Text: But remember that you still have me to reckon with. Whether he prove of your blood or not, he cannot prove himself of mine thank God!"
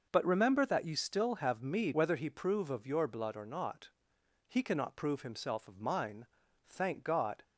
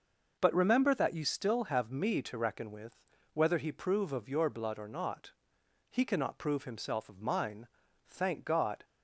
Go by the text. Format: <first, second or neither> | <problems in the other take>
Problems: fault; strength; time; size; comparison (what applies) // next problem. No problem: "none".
second | skips "to reckon with"; at 1.9 s // pauses between "mine" and "thank"; at 6.2 s; 0.40 s long; also in the second